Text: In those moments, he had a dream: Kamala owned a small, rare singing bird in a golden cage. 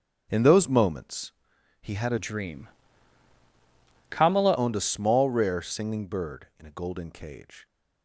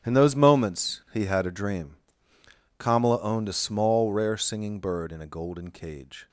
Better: second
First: starts louder than the rest; strong; until 1.3 s; 10 dB // changes voice from "dream" to "Kamala"; from 2.1 to 4.5 s; 2.4 s long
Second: starts louder than the rest; strong; until 1.1 s; 10.5 dB

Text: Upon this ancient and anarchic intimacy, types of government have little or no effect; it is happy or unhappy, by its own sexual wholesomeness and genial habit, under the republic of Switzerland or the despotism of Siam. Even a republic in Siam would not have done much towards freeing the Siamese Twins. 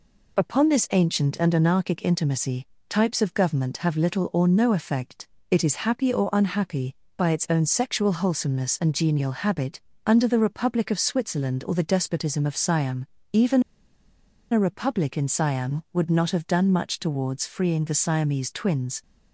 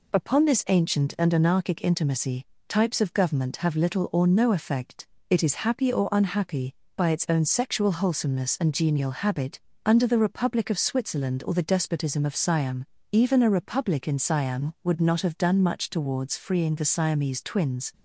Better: second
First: pauses between "Even" and "a"; noticeable; at 13.6 s; 0.90 s long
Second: none

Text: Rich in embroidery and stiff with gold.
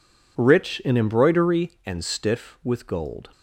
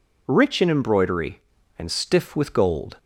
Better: neither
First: none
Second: none

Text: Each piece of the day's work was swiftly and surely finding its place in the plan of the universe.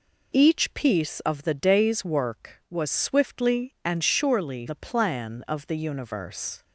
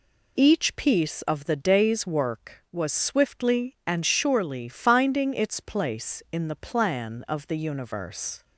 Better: second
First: skips "finding its place in"; at 4.6 s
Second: none

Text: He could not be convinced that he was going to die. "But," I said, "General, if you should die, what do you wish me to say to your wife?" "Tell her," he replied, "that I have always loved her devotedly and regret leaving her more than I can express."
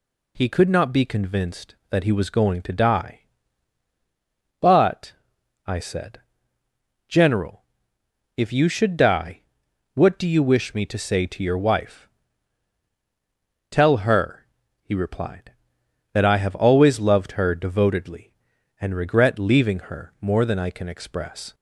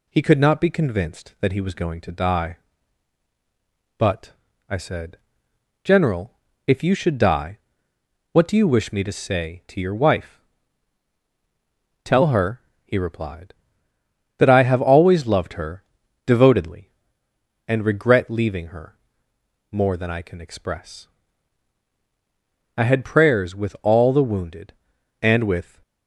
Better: first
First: none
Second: pauses between "her" and "devotedly"; at 15.8 s; 0.42 s long // pauses between "her" and "more"; noticeable; at 18.9 s; 0.76 s long // goes on to say "I had prayers with all the wounded and with"; strong; from 22.7 s on; 3.0 s long

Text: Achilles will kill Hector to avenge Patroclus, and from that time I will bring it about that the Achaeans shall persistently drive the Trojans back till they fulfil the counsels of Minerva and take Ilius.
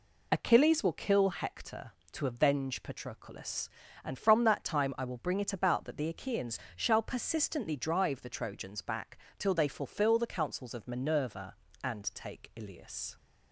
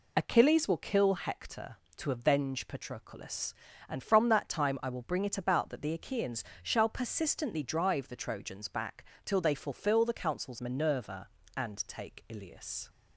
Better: first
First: pauses between "Achaeans" and "shall"; slight; at 6.5 s; 0.18 s long // pauses between "back" and "till"; slight; at 9.1 s; 0.20 s long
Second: pauses between "Achaeans" and "shall"; slight; at 6.4 s; 0.20 s long // pauses between "back" and "till"; slight; at 9.0 s; 0.20 s long // skips "of"; at 10.5 s

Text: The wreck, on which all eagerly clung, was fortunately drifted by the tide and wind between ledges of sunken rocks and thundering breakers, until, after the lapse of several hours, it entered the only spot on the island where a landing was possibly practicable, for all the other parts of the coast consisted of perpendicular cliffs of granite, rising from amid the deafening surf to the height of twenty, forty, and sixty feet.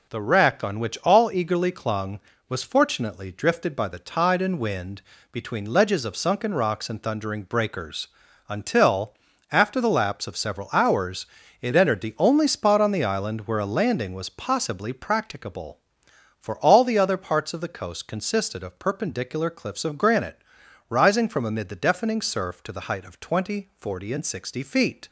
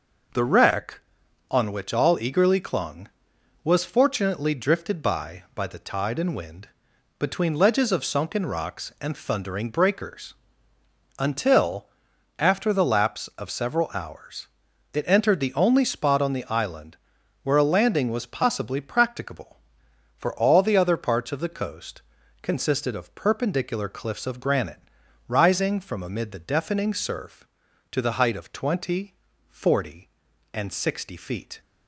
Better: first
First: pauses between "wind" and "between"; slight; at 5.0 s; 0.30 s long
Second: says "by" twice; at 5.5 s // pauses between "wind" and "between"; noticeable; at 6.6 s; 0.50 s long // pauses between "island" and "where"; noticeable; at 16.9 s; 0.46 s long // pauses between "coast" and "consisted"; at 22.0 s; 0.38 s long

